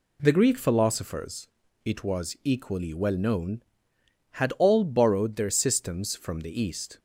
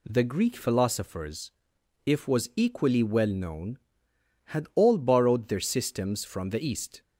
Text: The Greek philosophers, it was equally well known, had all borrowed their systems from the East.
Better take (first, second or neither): first